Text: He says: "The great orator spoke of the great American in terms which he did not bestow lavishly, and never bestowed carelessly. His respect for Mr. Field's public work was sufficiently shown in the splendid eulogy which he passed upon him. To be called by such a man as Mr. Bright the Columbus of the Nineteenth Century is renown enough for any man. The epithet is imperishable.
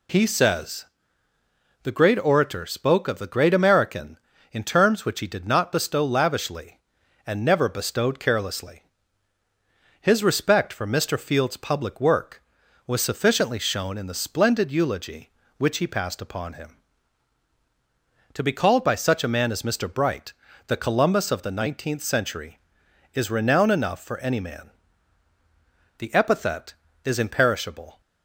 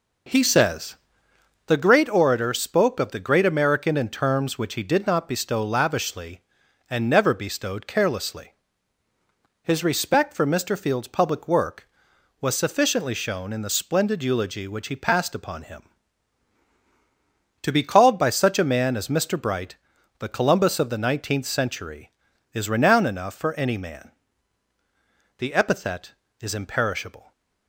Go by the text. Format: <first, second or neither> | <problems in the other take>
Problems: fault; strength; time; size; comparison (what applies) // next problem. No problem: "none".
first | starts louder than the rest; noticeable; until 2.0 s; 5 dB // pauses between "Bright" and "the"; at 19.7 s; 0.42 s long; slight in the first